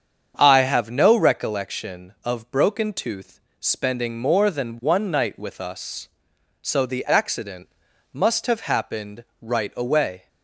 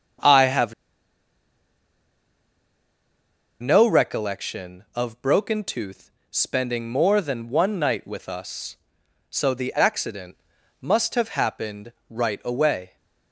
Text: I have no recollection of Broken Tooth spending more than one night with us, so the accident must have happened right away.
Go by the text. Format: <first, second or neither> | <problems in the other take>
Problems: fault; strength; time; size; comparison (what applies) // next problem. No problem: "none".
first | starts louder than the rest; strong; until 4.1 s; 7.5 dB; strong in the first // pauses between "have" and "no"; strong; at 0.7 s; 2.8 s long // pauses between "Tooth" and "spending"; slight; at 6.1 s; 0.22 s long; slight in the first // pauses between "accident" and "must"; at 10.3 s; 0.44 s long; also in the first // pauses between "happened" and "right"; slight; at 11.9 s; 0.18 s long; slight in the first